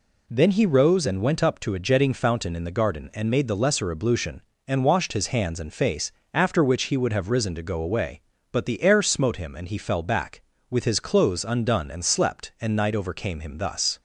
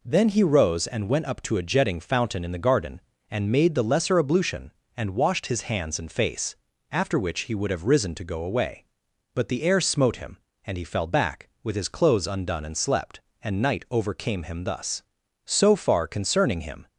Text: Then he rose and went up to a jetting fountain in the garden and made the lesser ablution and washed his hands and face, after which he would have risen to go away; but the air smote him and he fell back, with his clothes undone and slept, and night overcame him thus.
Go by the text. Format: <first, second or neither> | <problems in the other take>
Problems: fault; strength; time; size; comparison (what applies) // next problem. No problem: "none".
first | goes on to say "So far concerning him"; from 15.4 s on; 1.4 s long